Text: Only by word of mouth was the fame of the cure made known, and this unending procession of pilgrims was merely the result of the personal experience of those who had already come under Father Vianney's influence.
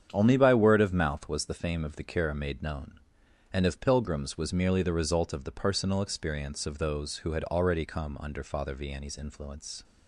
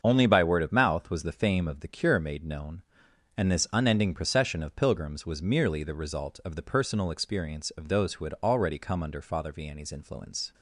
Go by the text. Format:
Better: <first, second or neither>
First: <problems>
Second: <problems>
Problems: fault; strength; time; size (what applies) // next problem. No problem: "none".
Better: second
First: starts louder than the rest; strong; until 1.1 s; 8.5 dB // skips "this unending procession"; at 3.6 s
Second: starts louder than the rest; until 1.0 s; 7 dB